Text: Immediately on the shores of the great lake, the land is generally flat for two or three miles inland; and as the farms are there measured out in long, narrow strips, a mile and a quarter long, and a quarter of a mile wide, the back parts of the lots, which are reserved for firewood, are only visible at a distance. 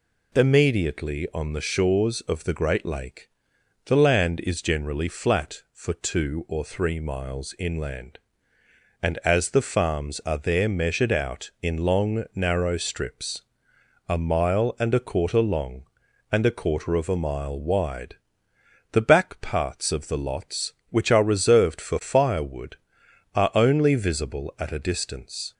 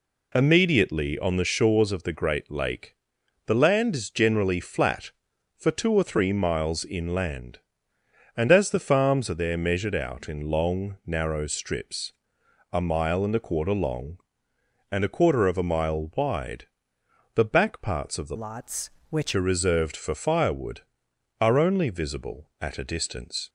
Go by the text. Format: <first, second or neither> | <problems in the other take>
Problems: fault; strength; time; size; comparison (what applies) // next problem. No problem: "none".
first | changes voice from "lots" to "which"; from 18.3 to 19.3 s; 1.0 s long